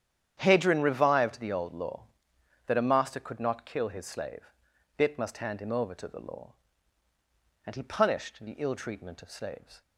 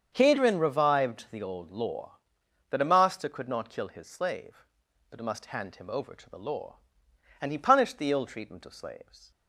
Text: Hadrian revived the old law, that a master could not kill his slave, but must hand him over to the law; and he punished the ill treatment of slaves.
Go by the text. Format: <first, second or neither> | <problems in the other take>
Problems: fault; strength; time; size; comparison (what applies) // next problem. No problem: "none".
second | starts louder than the rest; strong; until 1.3 s; 9.5 dB; strong in the second // says "bit" for "but"; at 4.9 s